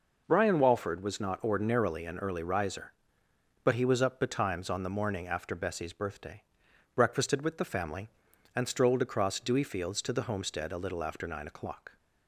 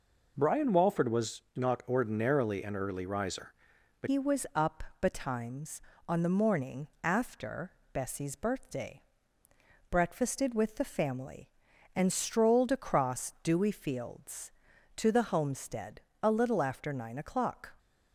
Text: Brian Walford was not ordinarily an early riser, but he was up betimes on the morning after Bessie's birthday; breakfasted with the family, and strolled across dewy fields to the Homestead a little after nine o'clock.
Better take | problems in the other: first | changes voice at "he"; from 4.0 s on; 13.7 s long // pauses between "up" and "betimes"; slight; at 4.8 s; 0.18 s long // pauses between "morning" and "after"; slight; at 6.8 s; 0.16 s long // pauses between "after" and "Bessie's"; slight; at 7.6 s; 0.24 s long // pauses between "Homestead" and "a"; slight; at 15.9 s; 0.24 s long

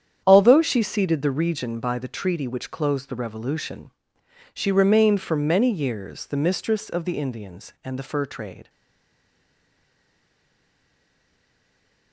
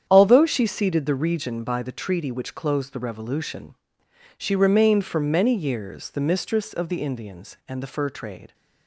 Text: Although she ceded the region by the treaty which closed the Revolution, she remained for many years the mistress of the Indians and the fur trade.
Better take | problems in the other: second | starts louder than the rest; strong; until 1.2 s; 9 dB; strong in the second // stays silent after the last word; strong; from 8.6 s on; 3.5 s long

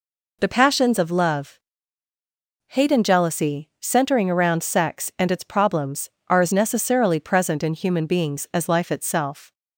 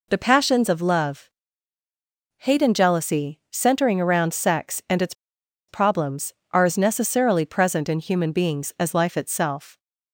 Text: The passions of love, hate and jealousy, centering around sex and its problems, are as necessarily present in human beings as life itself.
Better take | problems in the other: first | pauses between "its" and "problems"; noticeable; at 5.1 s; 0.56 s long

